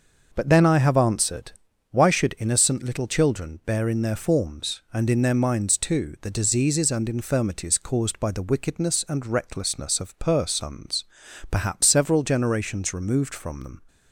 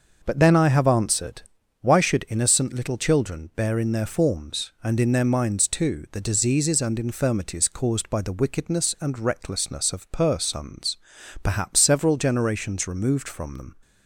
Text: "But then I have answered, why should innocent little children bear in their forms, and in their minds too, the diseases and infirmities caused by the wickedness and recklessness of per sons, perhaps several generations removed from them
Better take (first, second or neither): neither